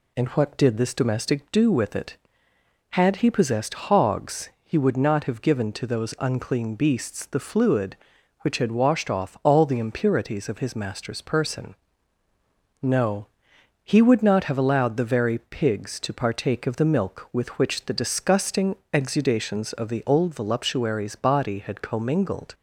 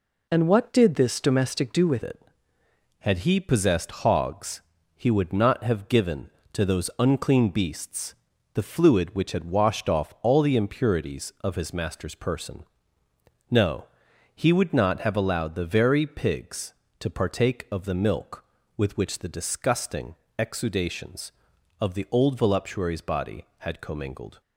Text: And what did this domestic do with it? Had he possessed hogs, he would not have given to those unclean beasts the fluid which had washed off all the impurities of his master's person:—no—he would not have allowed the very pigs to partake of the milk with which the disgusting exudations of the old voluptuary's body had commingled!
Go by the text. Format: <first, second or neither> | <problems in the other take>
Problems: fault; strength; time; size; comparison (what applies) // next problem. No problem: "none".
first | changes voice at "it"; from 2.0 s on; 22.4 s long // pauses between "beasts" and "the"; at 8.1 s; 0.40 s long // pauses between "disgusting" and "exudations"; slight; at 20.1 s; 0.24 s long; slight in the first